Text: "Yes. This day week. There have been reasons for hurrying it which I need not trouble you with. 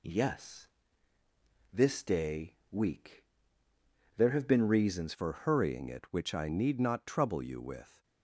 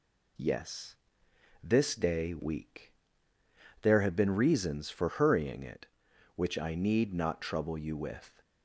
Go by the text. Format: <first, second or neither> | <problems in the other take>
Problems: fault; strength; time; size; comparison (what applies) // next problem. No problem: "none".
second | changes voice at "for"; from 5.1 s on; 2.9 s long